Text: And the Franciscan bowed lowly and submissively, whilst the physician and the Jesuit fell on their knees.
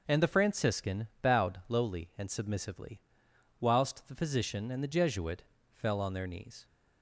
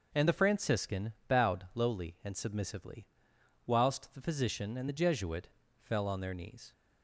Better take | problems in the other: neither | pauses between "Jesuit" and "fell"; slight; the same in both

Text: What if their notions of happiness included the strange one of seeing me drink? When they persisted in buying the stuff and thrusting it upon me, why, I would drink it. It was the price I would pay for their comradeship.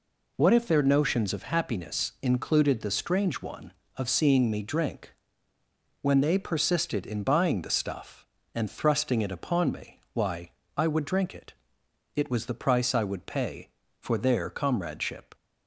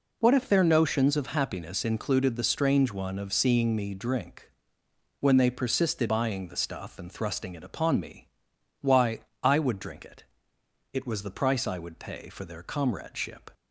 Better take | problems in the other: first | skips "in"; at 6.0 s

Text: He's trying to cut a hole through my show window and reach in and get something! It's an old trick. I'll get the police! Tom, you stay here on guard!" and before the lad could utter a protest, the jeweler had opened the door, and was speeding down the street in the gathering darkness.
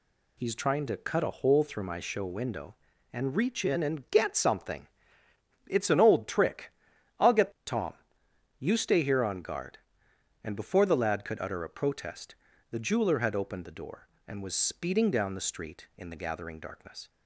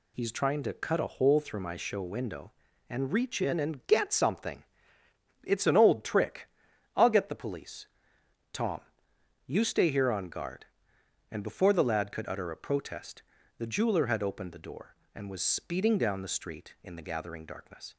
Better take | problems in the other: second | skips "the police"; at 7.5 s

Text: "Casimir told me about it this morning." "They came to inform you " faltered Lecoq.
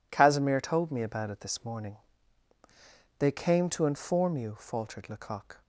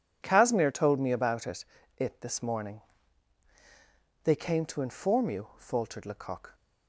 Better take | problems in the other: first | says "it" twice; at 1.9 s

